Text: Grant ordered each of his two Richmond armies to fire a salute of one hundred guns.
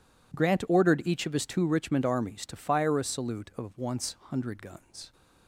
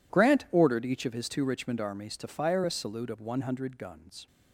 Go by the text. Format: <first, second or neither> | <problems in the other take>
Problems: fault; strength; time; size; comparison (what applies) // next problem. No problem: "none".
second | says "once" for "one"; at 3.7 s